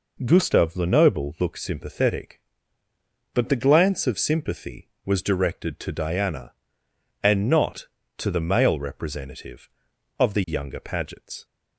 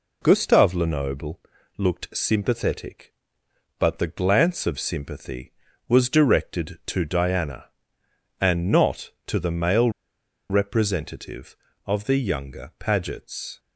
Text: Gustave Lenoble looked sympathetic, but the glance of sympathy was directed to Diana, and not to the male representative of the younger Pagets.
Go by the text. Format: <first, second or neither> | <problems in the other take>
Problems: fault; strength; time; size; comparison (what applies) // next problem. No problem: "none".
first | pauses between "Lenoble" and "looked"; at 1.3 s; 0.38 s long // pauses between "male" and "representative"; noticeable; at 9.8 s; 0.60 s long